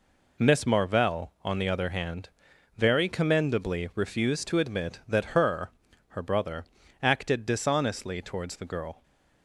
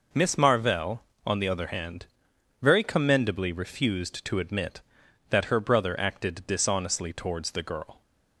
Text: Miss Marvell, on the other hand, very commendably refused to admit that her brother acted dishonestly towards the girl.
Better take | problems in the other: second | says "her" twice; at 6.0 s // pauses between "brother" and "acted"; at 6.6 s; 0.38 s long

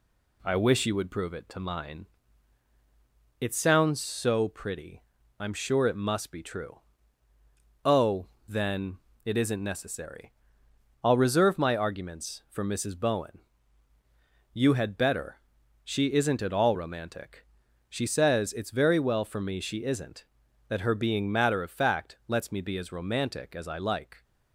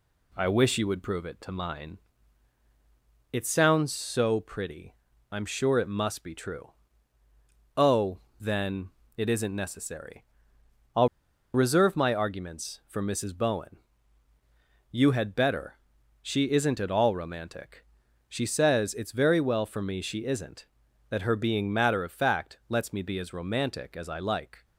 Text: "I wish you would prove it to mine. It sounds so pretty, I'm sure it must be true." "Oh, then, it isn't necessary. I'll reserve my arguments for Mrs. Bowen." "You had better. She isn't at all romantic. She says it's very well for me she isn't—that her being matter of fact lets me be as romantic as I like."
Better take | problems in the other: first | pauses between "I'll" and "reserve"; noticeable; at 11.0 s; 0.46 s long

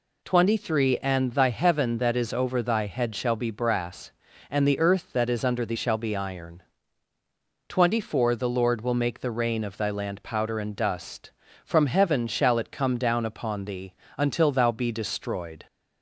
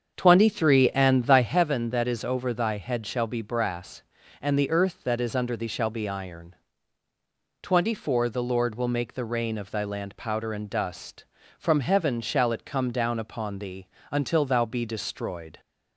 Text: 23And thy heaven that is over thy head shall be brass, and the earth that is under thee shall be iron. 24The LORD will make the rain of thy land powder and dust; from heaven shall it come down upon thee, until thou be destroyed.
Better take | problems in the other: first | starts louder than the rest; strong; until 1.6 s; 7 dB

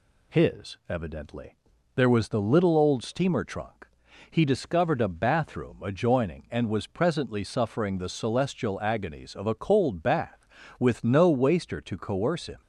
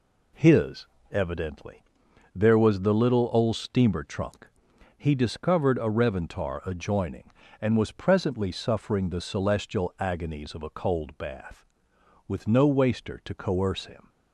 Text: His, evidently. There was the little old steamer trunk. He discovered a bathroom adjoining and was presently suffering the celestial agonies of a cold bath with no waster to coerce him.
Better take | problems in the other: first | says "reventar" for "bathroom"; at 5.9 s

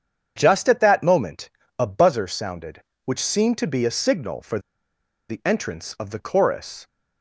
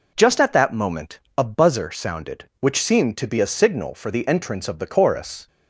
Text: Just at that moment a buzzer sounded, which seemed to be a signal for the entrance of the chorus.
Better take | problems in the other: second | starts louder than the rest; strong; until 1.3 s; 7.5 dB // pauses between "moment" and "a"; slight; at 1.4 s; 0.30 s long; slight in the second // pauses between "for" and "the"; noticeable; at 4.5 s; 0.70 s long

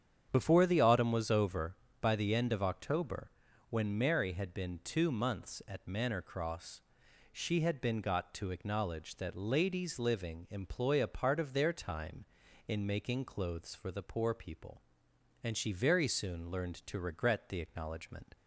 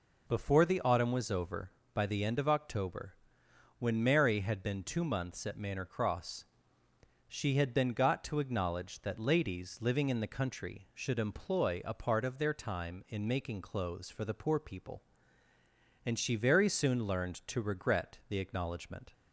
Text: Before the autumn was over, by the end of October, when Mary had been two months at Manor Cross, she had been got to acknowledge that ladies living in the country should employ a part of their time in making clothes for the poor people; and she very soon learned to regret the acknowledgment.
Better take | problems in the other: second | starts louder than the rest; strong; until 1.3 s; 8 dB // skips "in the country should"; at 10.4 s

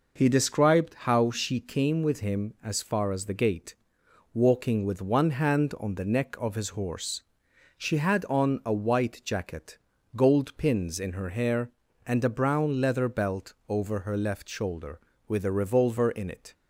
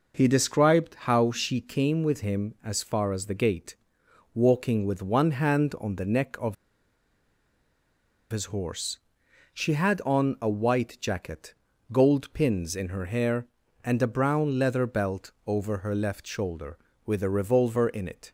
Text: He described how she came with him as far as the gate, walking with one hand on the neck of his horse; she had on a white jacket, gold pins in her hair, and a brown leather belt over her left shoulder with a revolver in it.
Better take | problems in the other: first | pauses between "of" and "his"; strong; at 6.5 s; 1.7 s long

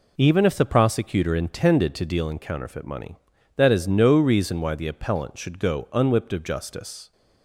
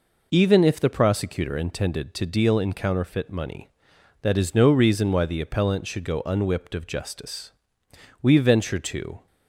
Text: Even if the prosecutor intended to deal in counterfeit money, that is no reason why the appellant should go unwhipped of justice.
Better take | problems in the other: first | goes on to say "We venture to"; noticeable; from 8.2 s on; 1.0 s long

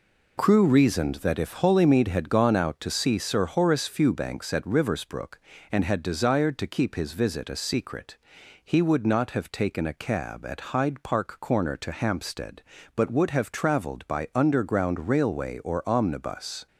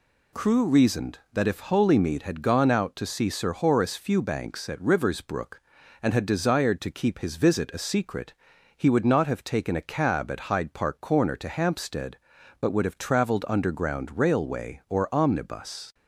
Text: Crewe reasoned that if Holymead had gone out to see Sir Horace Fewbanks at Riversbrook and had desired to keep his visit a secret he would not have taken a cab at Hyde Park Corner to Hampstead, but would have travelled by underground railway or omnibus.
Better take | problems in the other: first | pauses between "secret" and "he"; at 8.3 s; 0.42 s long; noticeable in the first // skips "by"; at 13.4 s

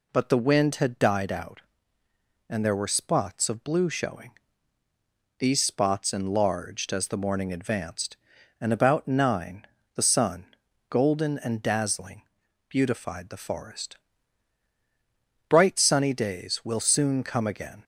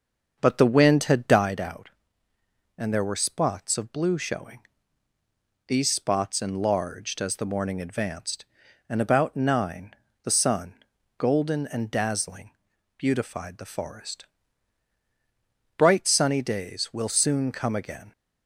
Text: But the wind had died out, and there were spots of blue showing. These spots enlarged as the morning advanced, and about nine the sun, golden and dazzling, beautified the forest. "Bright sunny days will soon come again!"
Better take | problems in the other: first | starts louder than the rest; until 1.5 s; 6.5 dB // pauses between "nine" and "the"; slight; at 9.9 s; 0.30 s long; slight in the first

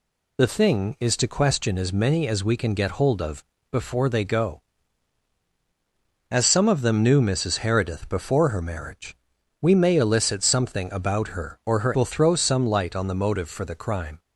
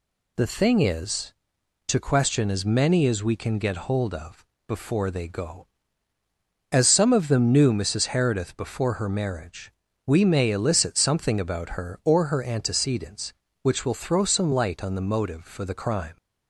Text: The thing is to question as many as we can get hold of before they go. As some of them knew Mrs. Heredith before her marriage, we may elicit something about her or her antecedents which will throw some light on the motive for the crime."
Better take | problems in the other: second | pauses between "of" and "before"; slight; at 3.4 s; 0.28 s long; slight in the second // skips "antecedents which"; at 11.9 s

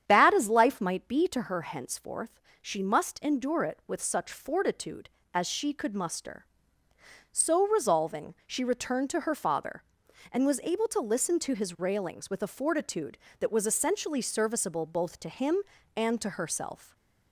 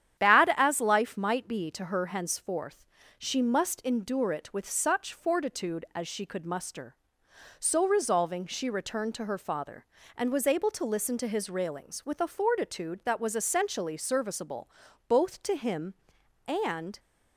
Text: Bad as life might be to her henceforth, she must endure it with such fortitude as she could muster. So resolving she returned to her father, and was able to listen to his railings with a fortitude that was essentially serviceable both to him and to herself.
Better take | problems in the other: first | starts louder than the rest; strong; until 1.2 s; 10 dB; strong in the first // pauses between "serviceable" and "both"; at 14.6 s; 0.40 s long // stops before "to herself"; at 16.9 s

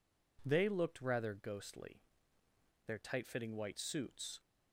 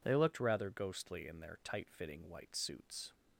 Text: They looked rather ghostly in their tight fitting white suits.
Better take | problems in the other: second | skips "in"; at 2.4 s

